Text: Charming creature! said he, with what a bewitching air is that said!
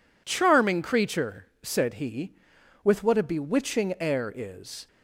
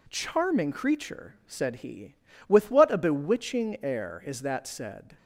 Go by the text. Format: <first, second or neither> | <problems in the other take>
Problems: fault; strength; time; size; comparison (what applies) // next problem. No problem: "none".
second | stops before "that said"; at 4.8 s